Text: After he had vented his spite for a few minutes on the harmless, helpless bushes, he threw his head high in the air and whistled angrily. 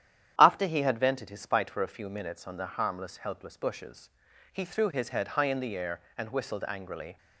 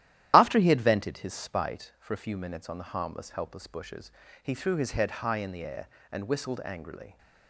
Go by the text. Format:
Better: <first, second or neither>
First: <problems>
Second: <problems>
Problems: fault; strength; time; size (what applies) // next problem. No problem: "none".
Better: first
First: starts louder than the rest; strong; until 1.3 s; 10.5 dB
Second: loses the start of "After"; at 0.3 s; 35 ms // starts louder than the rest; strong; until 1.3 s; 12.5 dB